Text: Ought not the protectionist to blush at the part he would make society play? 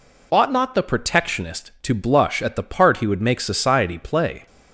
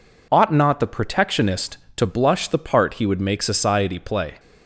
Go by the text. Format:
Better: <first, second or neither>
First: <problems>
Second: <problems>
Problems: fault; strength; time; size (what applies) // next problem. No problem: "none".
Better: first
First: none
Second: skips "at"; at 2.4 s